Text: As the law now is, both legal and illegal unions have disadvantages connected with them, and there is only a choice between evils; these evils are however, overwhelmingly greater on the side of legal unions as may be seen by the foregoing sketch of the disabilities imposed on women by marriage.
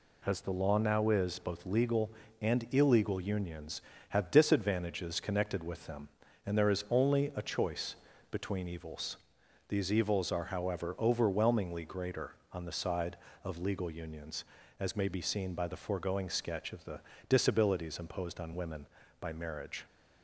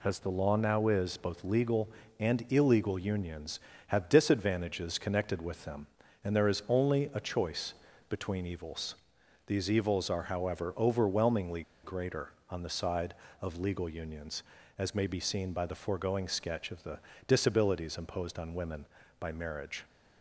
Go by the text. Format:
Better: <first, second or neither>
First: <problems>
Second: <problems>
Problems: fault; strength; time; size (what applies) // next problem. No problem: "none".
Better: first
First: pauses between "choice" and "between"; slight; at 7.9 s; 0.36 s long // pauses between "the" and "disabilities"; slight; at 16.9 s; 0.28 s long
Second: pauses between "choice" and "between"; slight; at 7.7 s; 0.36 s long // pauses between "overwhelmingly" and "greater"; slight; at 11.6 s; 0.22 s long // pauses between "the" and "disabilities"; slight; at 16.9 s; 0.28 s long